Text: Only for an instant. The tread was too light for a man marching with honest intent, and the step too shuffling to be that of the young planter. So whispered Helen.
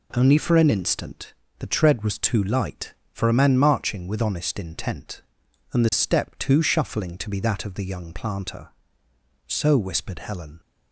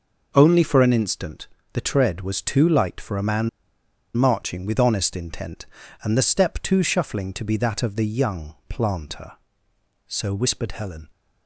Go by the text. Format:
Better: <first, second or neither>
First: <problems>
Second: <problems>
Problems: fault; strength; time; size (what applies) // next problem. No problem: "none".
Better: first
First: none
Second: pauses between "man" and "marching"; noticeable; at 3.4 s; 0.67 s long